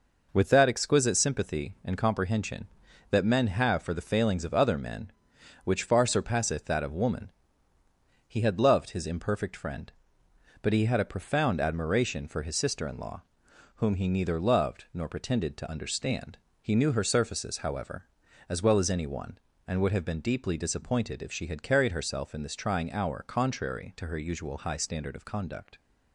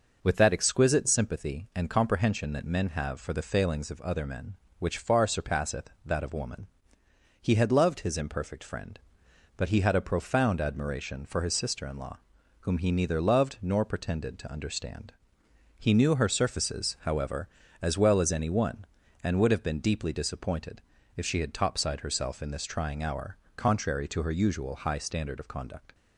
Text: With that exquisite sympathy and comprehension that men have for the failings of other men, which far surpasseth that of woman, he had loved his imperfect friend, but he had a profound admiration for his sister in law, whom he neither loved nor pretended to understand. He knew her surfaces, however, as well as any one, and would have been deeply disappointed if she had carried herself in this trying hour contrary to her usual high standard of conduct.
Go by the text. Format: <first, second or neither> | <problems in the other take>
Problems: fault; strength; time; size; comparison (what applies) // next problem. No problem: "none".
first | pauses between "disappointed" and "if"; slight; at 20.8 s; 0.34 s long // says "topside" for "carried"; at 21.5 s // pauses between "hour" and "contrary"; slight; at 23.3 s; 0.18 s long